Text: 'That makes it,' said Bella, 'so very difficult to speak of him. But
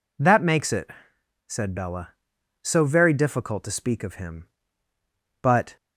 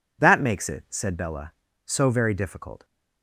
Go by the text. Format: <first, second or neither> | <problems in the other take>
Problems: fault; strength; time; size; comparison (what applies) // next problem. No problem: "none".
first | stops before "to speak of him But"; at 2.8 s